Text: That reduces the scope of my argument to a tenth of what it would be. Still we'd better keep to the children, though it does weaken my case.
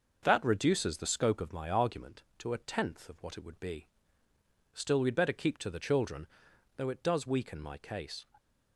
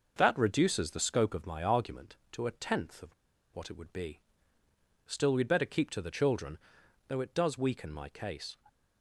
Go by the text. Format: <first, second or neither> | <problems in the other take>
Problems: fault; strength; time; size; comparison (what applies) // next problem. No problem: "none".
first | pauses between "of" and "what"; at 3.1 s; 0.40 s long